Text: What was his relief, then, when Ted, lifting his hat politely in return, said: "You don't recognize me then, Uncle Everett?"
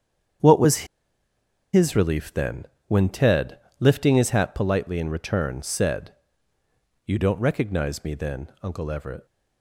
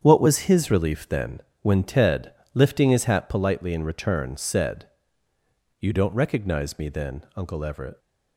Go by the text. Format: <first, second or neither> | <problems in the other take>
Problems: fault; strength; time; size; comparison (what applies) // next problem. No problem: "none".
second | starts louder than the rest; strong; until 2.3 s; 8 dB; strong in the second // pauses between "was" and "his"; noticeable; at 0.8 s; 0.88 s long